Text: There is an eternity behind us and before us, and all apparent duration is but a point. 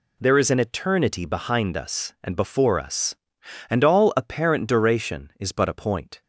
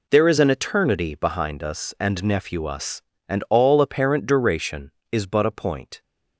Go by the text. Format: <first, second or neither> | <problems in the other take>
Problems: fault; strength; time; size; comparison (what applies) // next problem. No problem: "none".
first | says "nephew" for "before"; at 2.2 s